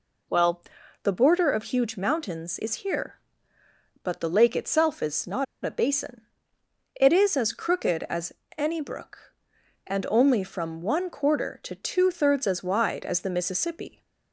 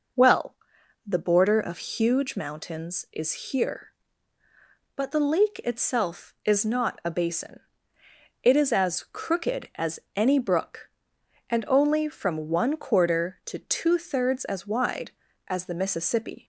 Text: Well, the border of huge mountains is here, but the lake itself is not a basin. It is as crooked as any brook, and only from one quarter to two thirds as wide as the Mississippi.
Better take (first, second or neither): second